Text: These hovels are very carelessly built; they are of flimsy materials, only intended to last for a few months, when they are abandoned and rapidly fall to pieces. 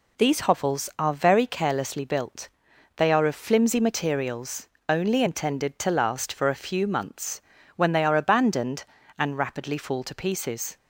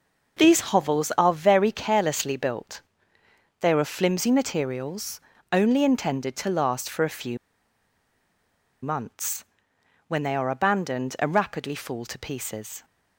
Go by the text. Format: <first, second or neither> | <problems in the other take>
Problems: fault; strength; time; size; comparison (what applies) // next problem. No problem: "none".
first | pauses between "few" and "months"; strong; at 7.3 s; 1.4 s long